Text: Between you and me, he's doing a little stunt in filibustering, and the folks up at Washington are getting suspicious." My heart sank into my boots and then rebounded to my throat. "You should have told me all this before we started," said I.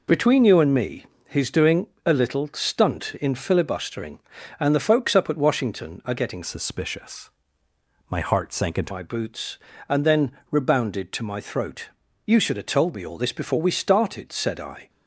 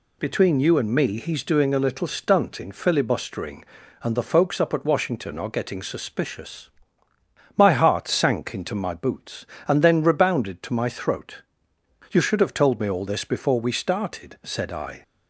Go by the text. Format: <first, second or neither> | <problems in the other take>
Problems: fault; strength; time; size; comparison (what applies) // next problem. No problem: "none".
second | pauses between "doing" and "a"; slight; at 1.8 s; 0.18 s long // changes voice from "suspicious" to "into"; from 6.4 to 8.9 s; 2.5 s long // pauses between "then" and "rebounded"; slight; at 10.3 s; 0.18 s long